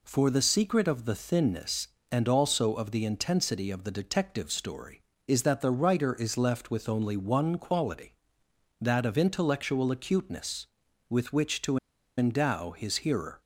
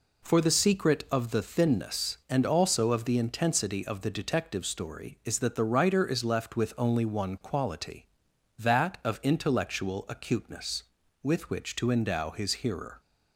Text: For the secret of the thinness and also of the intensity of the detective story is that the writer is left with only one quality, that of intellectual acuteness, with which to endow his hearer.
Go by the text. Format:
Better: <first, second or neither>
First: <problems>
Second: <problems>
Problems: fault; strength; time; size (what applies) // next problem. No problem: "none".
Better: second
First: pauses between "to" and "endow"; at 11.7 s; 0.39 s long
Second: none